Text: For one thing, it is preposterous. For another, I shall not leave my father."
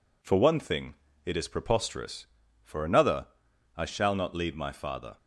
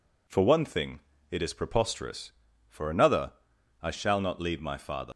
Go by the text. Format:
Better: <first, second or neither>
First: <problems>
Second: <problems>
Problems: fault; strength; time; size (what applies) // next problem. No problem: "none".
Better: first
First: none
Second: leaves "father" unfinished; at 5.1 s; 100 ms